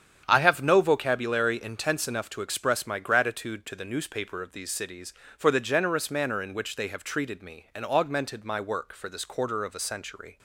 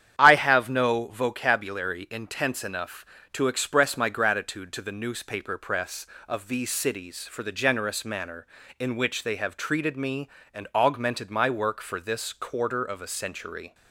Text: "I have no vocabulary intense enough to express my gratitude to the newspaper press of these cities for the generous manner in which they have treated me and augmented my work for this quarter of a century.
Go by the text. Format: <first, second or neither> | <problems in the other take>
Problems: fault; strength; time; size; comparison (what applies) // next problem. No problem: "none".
second | starts louder than the rest; strong; until 1.2 s; 8.5 dB; strong in the second // skips "press"; at 4.4 s